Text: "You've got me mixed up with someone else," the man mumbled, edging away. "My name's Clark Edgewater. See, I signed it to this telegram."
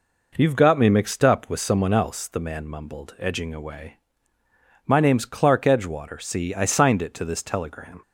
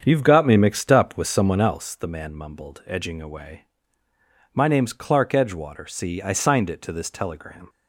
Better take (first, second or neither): first